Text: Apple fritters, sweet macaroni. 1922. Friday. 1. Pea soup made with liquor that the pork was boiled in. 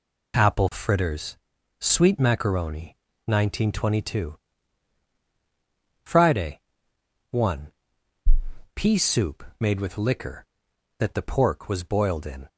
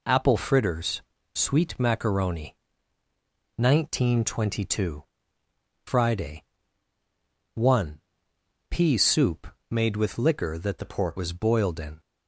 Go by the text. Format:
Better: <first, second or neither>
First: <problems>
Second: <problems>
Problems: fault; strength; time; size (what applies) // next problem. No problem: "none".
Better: first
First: none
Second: pauses between "soup" and "made"; slight; at 9.4 s; 0.24 s long // changes voice from "the" to "pork"; from 10.7 to 11.1 s; 0.4 s long